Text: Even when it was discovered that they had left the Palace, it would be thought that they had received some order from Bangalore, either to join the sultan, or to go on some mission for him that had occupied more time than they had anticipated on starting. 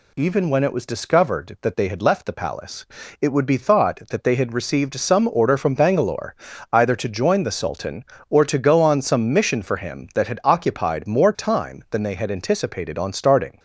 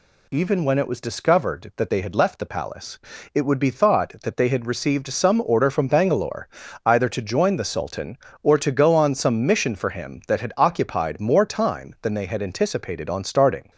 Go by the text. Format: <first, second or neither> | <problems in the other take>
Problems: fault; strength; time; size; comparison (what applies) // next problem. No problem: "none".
neither | none